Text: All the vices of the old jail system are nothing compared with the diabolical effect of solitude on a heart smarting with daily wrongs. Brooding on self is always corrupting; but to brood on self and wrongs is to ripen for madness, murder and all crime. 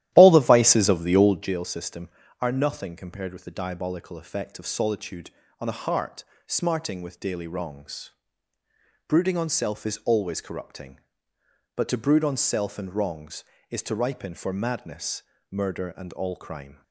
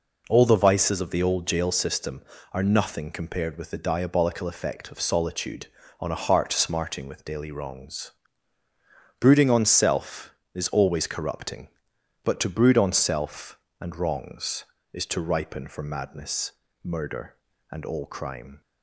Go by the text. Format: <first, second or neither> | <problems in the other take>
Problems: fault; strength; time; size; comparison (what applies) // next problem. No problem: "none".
second | starts louder than the rest; strong; until 1.6 s; 13.5 dB // pauses between "heart" and "smarting"; slight; at 6.2 s; 0.22 s long